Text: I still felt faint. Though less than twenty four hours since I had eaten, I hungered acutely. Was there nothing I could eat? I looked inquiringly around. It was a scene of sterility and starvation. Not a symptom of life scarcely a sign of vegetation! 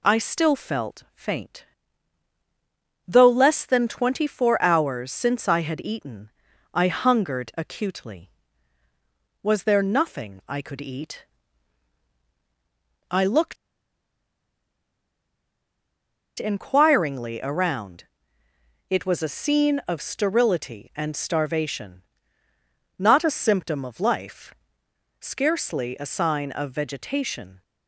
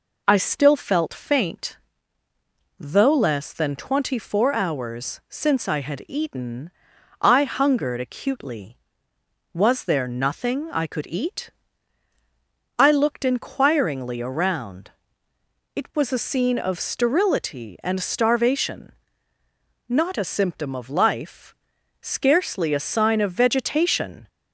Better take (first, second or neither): second